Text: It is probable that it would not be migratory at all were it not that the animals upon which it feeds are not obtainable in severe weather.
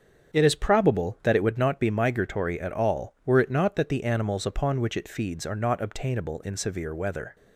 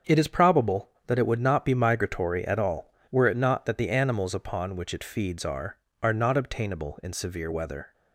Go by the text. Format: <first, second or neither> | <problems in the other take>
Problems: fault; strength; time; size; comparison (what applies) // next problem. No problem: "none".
first | starts louder than the rest; until 1.2 s; 7 dB; strong in the first // says "are" twice; at 6.0 s